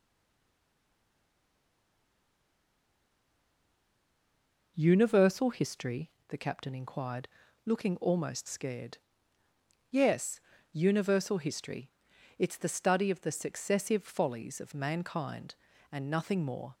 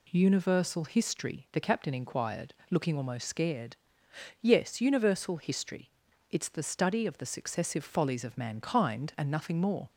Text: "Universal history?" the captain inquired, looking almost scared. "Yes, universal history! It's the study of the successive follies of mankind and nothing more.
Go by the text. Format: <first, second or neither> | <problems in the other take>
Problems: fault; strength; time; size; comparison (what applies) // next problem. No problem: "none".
second | stays silent before the first word; strong; until 4.7 s; 4.7 s long